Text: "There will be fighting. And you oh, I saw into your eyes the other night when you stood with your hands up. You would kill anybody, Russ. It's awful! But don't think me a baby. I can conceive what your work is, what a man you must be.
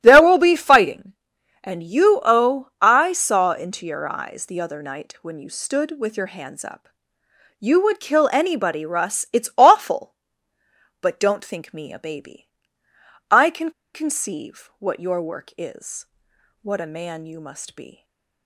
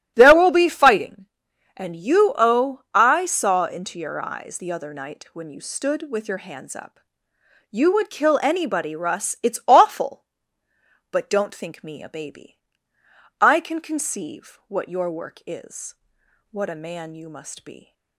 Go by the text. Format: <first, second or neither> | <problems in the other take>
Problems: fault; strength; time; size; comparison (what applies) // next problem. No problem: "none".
second | starts louder than the rest; strong; until 1.0 s; 12.5 dB; strong in the second // pauses between "can" and "conceive"; slight; at 13.7 s; 0.22 s long // stays silent after the last word; slight; from 17.9 s on; 0.5 s long